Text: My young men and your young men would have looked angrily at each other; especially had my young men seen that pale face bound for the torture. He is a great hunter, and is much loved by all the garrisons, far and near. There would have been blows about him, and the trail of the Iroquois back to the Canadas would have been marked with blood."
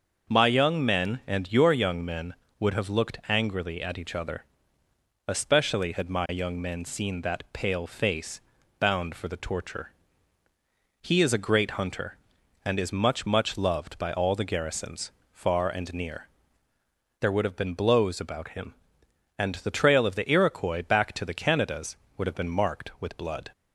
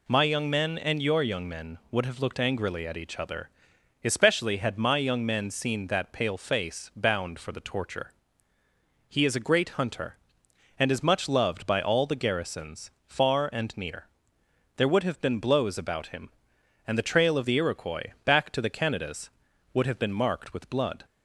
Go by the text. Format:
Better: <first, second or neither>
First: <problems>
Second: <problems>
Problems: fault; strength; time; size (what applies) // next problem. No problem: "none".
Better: second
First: starts louder than the rest; until 1.3 s; 6.5 dB // pauses between "face" and "bound"; slight; at 8.4 s; 0.36 s long // says "much" twice; at 13.2 s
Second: none